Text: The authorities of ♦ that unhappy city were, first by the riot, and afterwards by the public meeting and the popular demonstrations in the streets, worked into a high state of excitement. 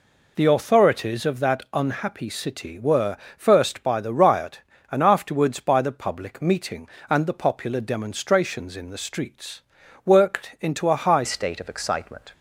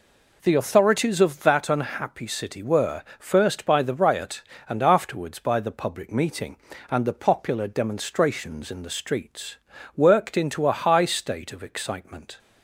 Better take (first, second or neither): second